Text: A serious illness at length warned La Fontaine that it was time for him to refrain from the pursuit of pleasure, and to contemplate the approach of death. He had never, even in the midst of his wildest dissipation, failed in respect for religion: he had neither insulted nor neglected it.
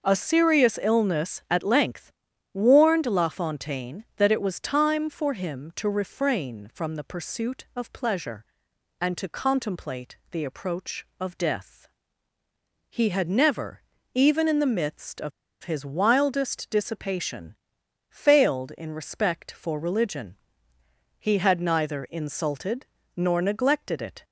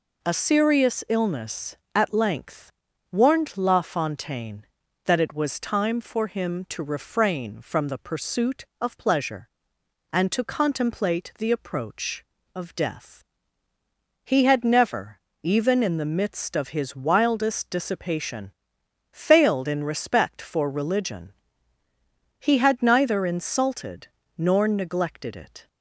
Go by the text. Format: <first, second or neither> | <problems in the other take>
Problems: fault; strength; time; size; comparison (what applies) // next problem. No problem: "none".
second | starts louder than the rest; noticeable; until 1.0 s; 6 dB // pauses between "length" and "warned"; at 2.1 s; 0.42 s long; also in the second // pauses between "contemplate" and "the"; slight; at 10.1 s; 0.16 s long // pauses between "of" and "his"; slight; at 15.3 s; 0.32 s long // pauses between "insulted" and "nor"; slight; at 22.8 s; 0.30 s long; slight in the second